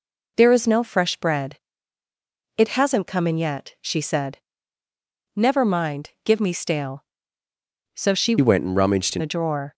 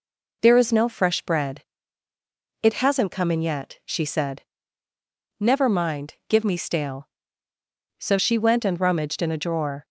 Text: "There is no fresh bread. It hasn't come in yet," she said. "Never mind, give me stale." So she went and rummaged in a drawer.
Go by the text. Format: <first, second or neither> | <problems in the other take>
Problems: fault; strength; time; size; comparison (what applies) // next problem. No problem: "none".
second | changes voice from "went" to "in"; from 8.4 to 9.2 s; 0.8 s long